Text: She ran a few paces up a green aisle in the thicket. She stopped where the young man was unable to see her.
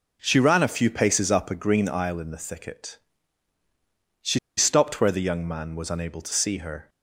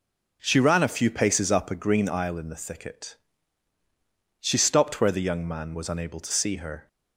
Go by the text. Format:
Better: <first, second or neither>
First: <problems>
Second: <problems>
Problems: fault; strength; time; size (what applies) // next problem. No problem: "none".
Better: second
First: pauses between "She" and "stopped"; slight; at 4.3 s; 0.18 s long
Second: none